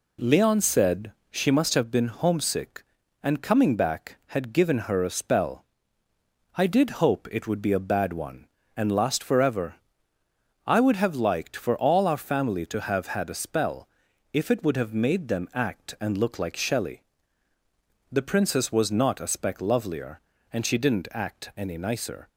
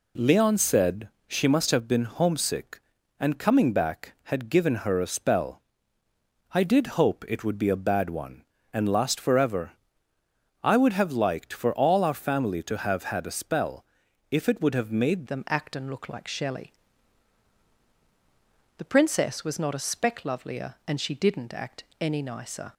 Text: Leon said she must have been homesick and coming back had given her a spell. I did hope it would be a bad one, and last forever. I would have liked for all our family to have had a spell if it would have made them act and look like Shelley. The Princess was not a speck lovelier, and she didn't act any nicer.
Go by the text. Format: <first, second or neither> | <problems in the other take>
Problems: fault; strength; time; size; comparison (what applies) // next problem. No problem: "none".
first | pauses between "said" and "she"; slight; at 1.1 s; 0.18 s long; slight in the first // pauses between "spell" and "if"; noticeable; at 13.8 s; 0.46 s long; also in the first // changes voice at "them"; from 15.2 s on; 7.5 s long // pauses between "act" and "any"; slight; at 21.8 s; 0.18 s long